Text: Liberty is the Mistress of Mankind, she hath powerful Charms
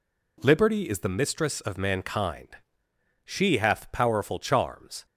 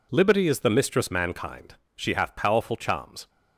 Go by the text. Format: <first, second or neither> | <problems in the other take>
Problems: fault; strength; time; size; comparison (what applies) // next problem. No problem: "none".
first | skips "of"; at 1.1 s